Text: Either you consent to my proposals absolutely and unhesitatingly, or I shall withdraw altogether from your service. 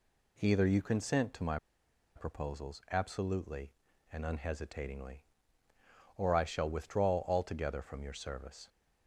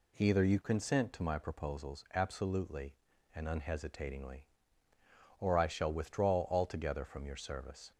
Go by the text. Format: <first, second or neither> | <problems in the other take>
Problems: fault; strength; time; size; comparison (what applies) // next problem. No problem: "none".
second | pauses between "my" and "proposals"; noticeable; at 1.5 s; 0.58 s long